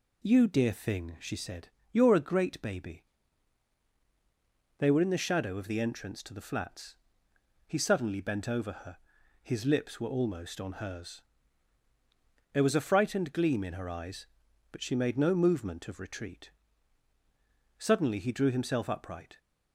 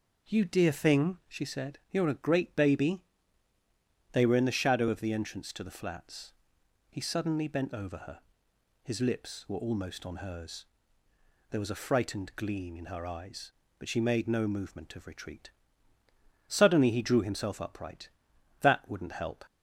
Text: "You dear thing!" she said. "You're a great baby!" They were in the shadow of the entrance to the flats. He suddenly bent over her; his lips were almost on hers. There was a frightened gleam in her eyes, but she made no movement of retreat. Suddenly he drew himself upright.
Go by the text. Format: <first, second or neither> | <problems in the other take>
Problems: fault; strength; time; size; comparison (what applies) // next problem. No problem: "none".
first | goes on to say "That wouldn't help"; noticeable; from 18.6 s on; 0.82 s long